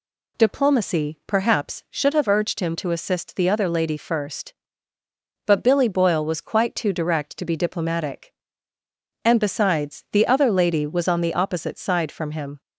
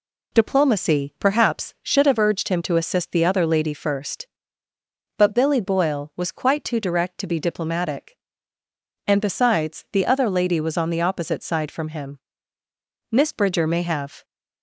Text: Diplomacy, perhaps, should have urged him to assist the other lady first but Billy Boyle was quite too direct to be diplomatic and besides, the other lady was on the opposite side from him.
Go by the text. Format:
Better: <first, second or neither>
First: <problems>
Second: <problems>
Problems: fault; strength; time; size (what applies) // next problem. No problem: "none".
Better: first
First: none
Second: goes on to say "Miss Bridger may have"; noticeable; from 13.1 s on; 1.1 s long